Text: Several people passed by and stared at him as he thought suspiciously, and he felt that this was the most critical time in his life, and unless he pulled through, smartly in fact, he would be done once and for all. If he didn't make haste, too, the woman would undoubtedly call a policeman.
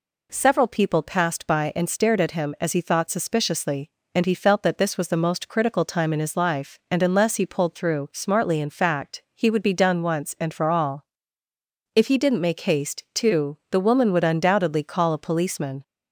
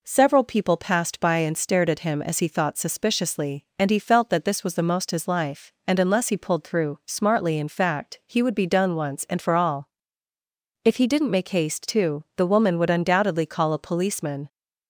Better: first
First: none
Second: skips "critical time in"; at 5.1 s

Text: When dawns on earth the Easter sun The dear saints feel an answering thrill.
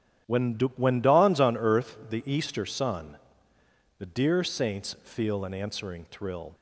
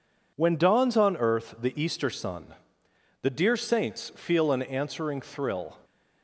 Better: second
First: starts louder than the rest; strong; until 1.5 s; 12 dB // says "When" twice; at 0.7 s // pauses between "sun" and "The"; noticeable; at 3.1 s; 0.80 s long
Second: pauses between "sun" and "The"; noticeable; at 2.5 s; 0.66 s long

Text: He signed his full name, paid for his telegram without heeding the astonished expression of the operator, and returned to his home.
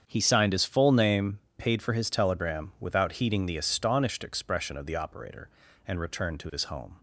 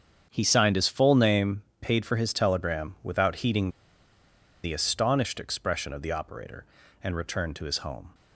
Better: first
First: starts louder than the rest; strong; until 1.0 s; 7.5 dB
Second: starts louder than the rest; strong; until 1.3 s; 7.5 dB // pauses between "heeding" and "the"; noticeable; at 3.6 s; 0.94 s long

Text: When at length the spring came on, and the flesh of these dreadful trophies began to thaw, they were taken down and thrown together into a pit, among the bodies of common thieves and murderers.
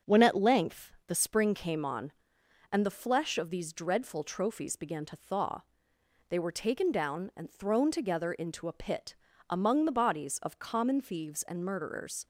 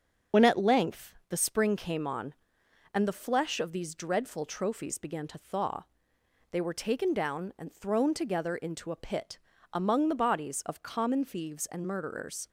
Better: first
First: starts louder than the rest; until 1.2 s; 7 dB // pauses between "length" and "the"; slight; at 0.9 s; 0.16 s long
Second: loses the start of "When"; at 0.3 s; 65 ms // starts louder than the rest; until 1.5 s; 7 dB // pauses between "length" and "the"; slight; at 1.1 s; 0.16 s long

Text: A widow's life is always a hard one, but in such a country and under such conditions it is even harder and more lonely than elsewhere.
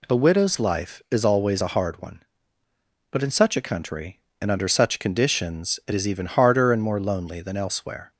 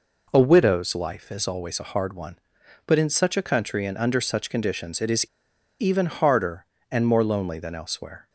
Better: first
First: none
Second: pauses between "is" and "even"; noticeable; at 5.2 s; 0.54 s long

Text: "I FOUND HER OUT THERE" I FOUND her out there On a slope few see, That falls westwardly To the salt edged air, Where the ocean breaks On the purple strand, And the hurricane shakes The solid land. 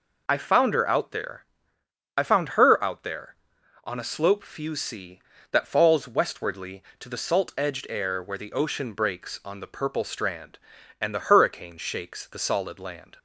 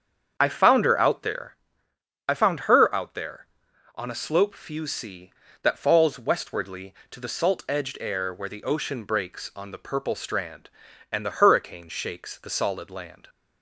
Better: first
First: pauses between "THERE" and "I"; noticeable; at 1.4 s; 0.74 s long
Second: starts louder than the rest; strong; until 1.5 s; 7.5 dB // pauses between "THERE" and "I"; noticeable; at 1.5 s; 0.74 s long

